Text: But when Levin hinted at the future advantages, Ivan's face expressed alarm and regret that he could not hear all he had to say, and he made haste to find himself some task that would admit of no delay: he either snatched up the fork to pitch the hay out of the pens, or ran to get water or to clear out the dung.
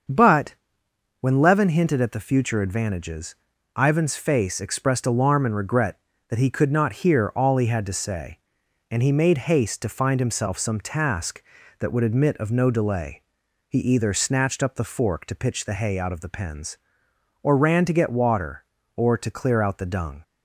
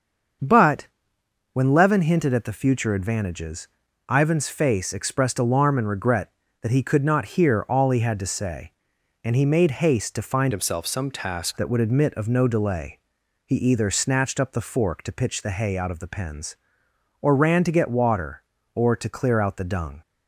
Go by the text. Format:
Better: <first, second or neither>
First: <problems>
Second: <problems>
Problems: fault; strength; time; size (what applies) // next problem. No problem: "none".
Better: first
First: starts louder than the rest; until 1.7 s; 6.5 dB // pauses between "But" and "when"; noticeable; at 0.5 s; 0.66 s long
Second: starts louder than the rest; until 2.0 s; 6.5 dB // pauses between "But" and "when"; noticeable; at 0.8 s; 0.66 s long // changes voice from "himself" to "task"; from 10.5 to 11.5 s; 1.0 s long